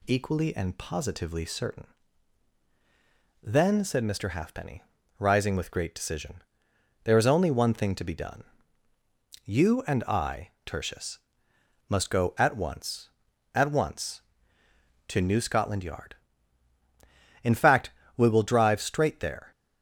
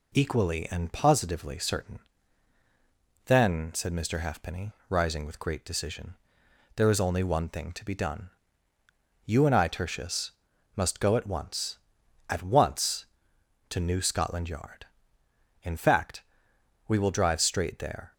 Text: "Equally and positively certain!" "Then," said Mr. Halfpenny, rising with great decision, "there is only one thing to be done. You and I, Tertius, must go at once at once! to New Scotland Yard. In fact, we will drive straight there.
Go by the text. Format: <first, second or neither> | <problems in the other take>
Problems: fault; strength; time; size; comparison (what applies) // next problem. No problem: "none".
neither | none